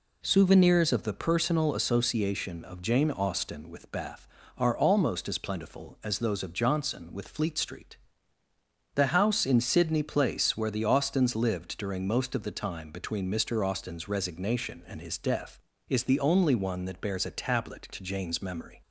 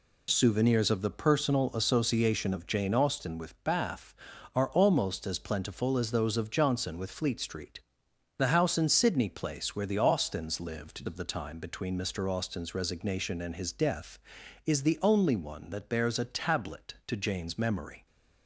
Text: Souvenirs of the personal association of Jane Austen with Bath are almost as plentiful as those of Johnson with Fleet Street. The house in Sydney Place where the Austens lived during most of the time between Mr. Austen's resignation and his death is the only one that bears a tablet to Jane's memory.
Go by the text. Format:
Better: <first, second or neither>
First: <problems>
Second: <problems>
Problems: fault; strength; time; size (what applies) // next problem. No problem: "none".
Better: first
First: none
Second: skips "during most"; at 11.0 s